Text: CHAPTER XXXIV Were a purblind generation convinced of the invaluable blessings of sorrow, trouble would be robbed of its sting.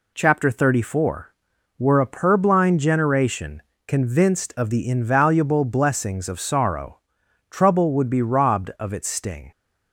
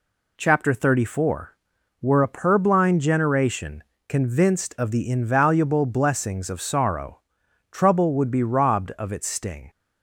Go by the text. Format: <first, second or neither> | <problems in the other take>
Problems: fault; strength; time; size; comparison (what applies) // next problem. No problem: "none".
neither | pauses between "generation" and "convinced"; slight; the same in both